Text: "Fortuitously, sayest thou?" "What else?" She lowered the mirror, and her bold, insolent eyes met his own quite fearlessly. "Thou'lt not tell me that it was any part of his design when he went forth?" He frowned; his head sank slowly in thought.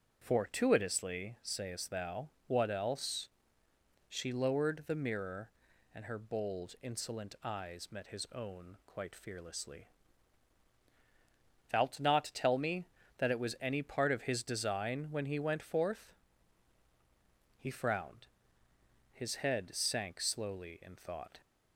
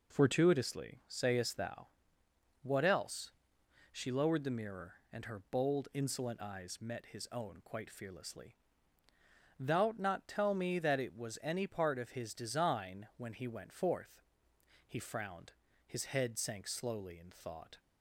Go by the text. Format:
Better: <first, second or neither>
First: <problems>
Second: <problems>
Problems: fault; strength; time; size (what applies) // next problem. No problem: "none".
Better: neither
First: none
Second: none